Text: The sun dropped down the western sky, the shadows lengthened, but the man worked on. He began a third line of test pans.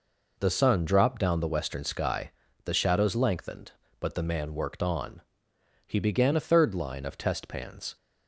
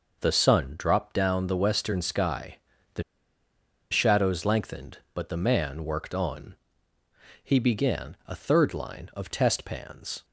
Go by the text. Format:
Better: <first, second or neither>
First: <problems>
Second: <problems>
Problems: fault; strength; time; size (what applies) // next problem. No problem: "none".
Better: first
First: none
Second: pauses between "the" and "shadows"; noticeable; at 3.0 s; 0.89 s long